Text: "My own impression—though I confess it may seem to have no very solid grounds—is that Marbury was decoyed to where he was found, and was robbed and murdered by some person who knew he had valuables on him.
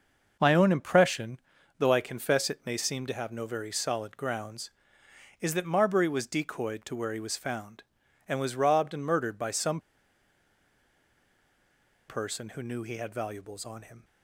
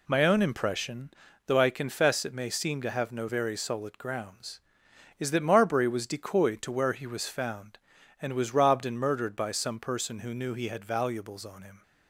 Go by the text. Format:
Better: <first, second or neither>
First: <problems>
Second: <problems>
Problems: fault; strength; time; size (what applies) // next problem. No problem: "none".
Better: second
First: pauses between "some" and "person"; strong; at 9.7 s; 2.2 s long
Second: none